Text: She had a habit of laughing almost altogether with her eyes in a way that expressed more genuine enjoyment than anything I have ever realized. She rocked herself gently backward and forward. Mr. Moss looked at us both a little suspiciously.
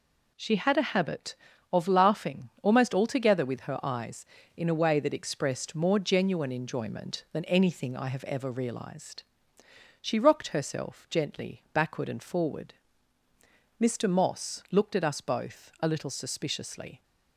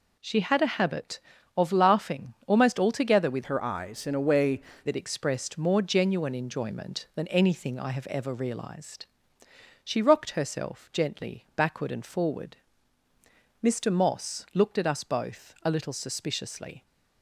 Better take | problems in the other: first | changes voice from "her" to "way"; from 3.4 to 4.6 s; 1.2 s long

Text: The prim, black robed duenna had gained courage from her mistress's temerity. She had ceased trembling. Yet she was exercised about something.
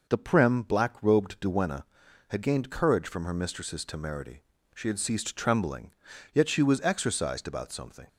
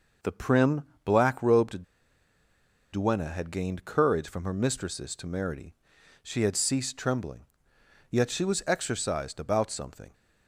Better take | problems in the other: first | pauses between "robed" and "duenna"; at 1.8 s; 1.0 s long

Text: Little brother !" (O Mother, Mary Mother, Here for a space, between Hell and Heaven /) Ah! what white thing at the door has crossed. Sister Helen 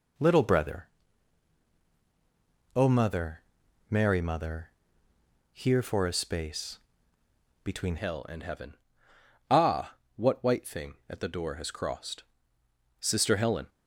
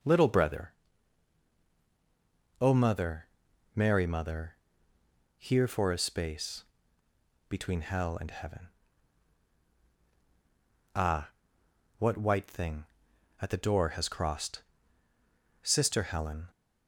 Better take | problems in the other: second | changes voice at "Hell"; from 7.9 s on; 5.7 s long

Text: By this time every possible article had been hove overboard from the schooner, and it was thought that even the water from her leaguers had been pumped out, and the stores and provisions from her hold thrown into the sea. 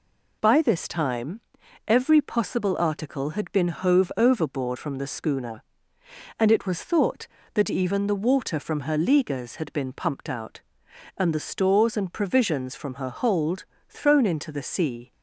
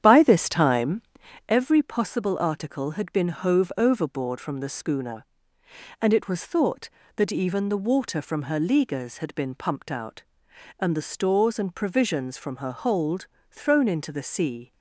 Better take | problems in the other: first | starts louder than the rest; strong; until 1.5 s; 9.5 dB // pauses between "time" and "every"; noticeable; at 1.0 s; 0.48 s long; noticeable in the first // pauses between "hold" and "thrown"; slight; at 13.2 s; 0.24 s long; slight in the first

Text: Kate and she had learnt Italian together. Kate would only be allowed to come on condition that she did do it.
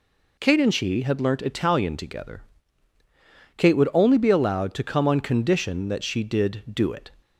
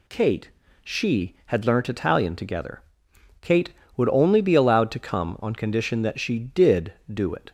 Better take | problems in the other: first | skips "and"; at 0.6 s

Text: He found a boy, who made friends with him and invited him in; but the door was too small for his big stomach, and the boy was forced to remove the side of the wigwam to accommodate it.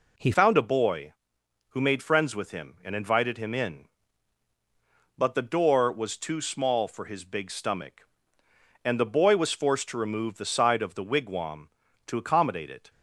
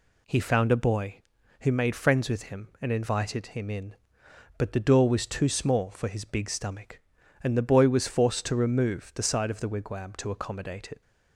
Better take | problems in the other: second | changes voice at "found"; from 0.3 s on; 12.5 s long

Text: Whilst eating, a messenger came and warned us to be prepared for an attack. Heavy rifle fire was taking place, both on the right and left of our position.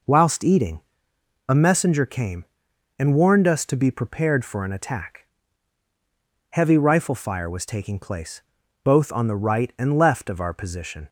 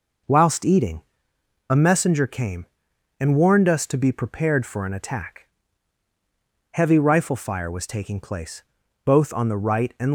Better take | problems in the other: first | stops before "left of our position"; at 10.0 s

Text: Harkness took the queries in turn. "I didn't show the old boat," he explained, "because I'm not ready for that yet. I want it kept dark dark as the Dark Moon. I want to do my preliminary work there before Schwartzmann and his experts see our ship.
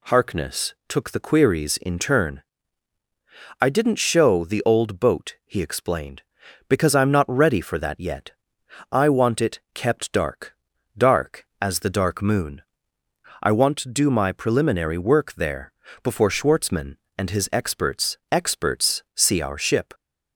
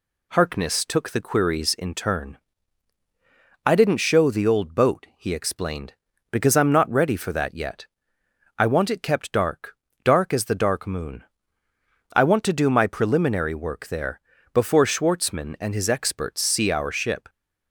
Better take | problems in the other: second | pauses between "dark" and "dark"; at 10.5 s; 0.42 s long; slight in the second // pauses between "there" and "before"; slight; at 15.7 s; 0.30 s long; slight in the second // says "experts" twice; at 18.3 s

